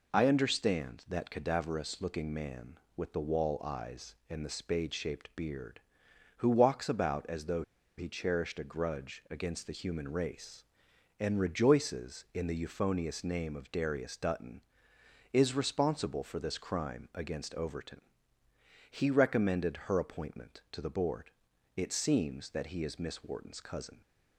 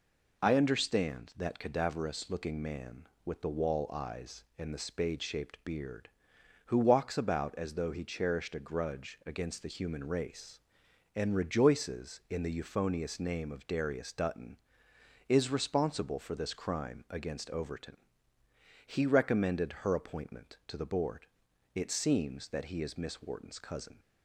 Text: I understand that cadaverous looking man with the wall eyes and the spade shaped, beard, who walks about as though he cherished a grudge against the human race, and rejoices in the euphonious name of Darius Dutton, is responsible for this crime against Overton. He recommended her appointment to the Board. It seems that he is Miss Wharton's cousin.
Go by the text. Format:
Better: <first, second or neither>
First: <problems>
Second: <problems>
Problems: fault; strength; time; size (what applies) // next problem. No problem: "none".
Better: second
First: pauses between "though" and "he"; slight; at 7.6 s; 0.35 s long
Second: none